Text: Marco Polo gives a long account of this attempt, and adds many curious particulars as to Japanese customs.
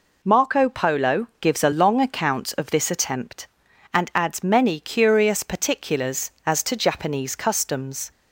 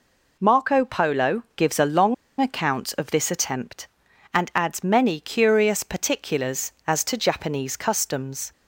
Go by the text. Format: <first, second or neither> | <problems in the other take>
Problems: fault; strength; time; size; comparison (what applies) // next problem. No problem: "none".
first | pauses between "long" and "account"; slight; at 2.1 s; 0.26 s long